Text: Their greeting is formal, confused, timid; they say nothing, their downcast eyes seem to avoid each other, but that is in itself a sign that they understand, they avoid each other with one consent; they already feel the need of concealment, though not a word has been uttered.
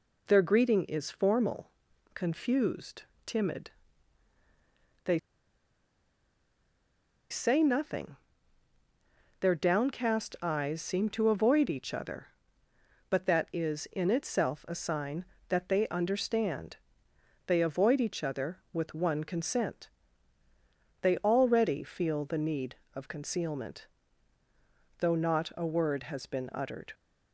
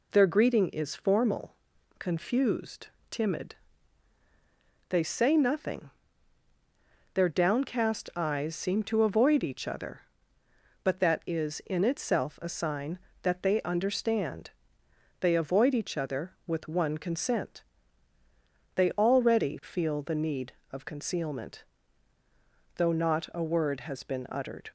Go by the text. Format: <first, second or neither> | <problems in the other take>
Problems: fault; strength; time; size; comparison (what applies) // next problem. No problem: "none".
second | pauses between "they" and "say"; strong; at 5.1 s; 2.1 s long